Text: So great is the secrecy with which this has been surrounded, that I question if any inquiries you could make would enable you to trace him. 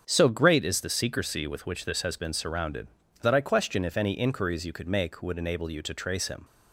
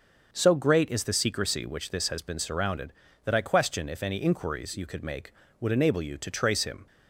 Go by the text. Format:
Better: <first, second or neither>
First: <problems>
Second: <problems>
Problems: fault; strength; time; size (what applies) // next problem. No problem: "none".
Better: first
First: starts louder than the rest; strong; until 1.0 s; 7.5 dB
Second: starts louder than the rest; until 1.3 s; 6.5 dB // skips "with"; at 1.6 s